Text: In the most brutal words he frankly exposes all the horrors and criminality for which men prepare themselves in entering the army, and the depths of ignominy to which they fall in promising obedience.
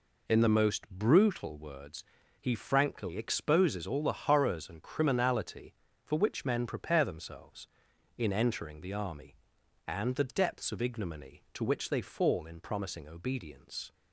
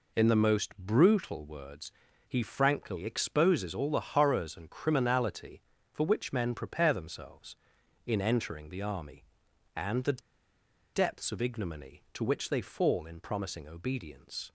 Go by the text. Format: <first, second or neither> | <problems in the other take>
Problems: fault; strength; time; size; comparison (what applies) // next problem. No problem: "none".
first | pauses between "words" and "he"; at 1.9 s; 0.38 s long; also in the first // pauses between "the" and "depths"; noticeable; at 10.1 s; 0.74 s long